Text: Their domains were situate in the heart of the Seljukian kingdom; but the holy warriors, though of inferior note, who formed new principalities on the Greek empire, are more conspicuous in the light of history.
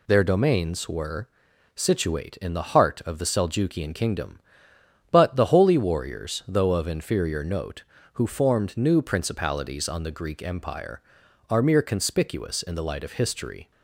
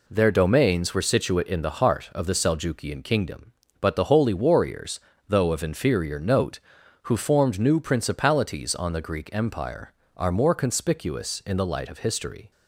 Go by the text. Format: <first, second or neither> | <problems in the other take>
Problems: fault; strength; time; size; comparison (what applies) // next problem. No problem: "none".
second | pauses between "were" and "situate"; noticeable; at 1.2 s; 0.48 s long // says "mere" for "more"; at 11.6 s